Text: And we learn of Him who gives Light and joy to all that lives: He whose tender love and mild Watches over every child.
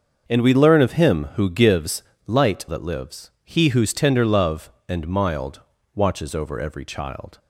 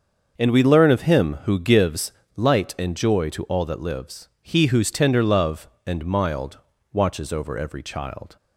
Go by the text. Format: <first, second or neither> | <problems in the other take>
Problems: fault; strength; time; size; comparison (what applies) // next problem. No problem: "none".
second | starts louder than the rest; until 1.2 s; 6.5 dB; also in the second // pauses between "gives" and "Light"; slight; at 2.0 s; 0.26 s long; slight in the second // skips "and joy to all"; at 2.6 s // pauses between "mild" and "Watches"; slight; at 5.6 s; 0.34 s long; slight in the second